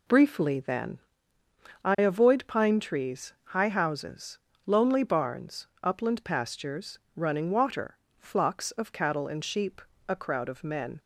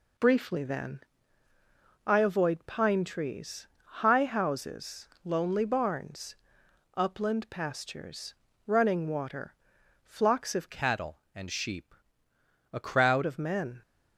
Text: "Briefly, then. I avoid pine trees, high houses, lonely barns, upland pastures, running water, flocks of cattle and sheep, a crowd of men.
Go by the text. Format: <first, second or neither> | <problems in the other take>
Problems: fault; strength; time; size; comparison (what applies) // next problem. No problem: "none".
first | changes voice from "cattle" to "crowd"; from 10.6 to 13.2 s; 2.6 s long